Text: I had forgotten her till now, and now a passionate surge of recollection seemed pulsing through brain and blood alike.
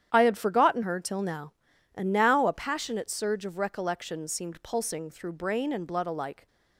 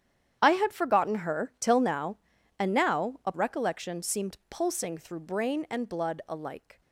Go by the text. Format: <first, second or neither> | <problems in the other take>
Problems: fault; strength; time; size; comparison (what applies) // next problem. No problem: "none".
first | starts louder than the rest; strong; until 1.4 s; 9.5 dB; strong in the first // skips "passionate surge of"; at 3.3 s